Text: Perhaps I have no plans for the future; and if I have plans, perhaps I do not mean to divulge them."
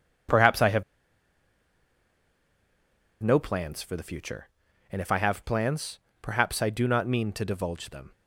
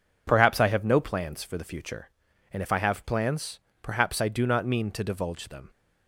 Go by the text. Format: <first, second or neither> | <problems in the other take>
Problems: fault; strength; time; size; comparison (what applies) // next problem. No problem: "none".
second | pauses between "have" and "no"; strong; at 0.8 s; 2.3 s long